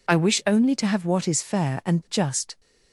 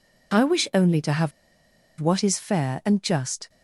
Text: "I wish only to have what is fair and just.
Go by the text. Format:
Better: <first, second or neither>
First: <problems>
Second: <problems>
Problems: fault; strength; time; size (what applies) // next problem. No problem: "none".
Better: first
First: none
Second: pauses between "have" and "what"; noticeable; at 1.3 s; 0.69 s long